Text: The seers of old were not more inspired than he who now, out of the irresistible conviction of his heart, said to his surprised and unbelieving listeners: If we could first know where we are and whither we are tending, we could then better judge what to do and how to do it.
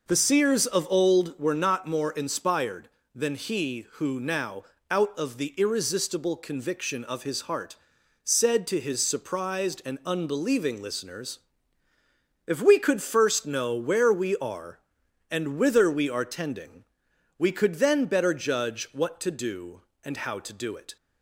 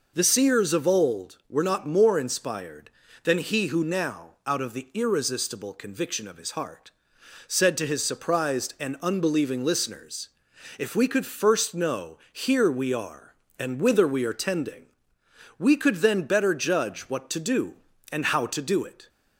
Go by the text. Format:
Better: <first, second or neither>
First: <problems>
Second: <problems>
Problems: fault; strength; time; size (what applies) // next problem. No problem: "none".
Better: first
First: none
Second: says "here" for "where"; at 12.3 s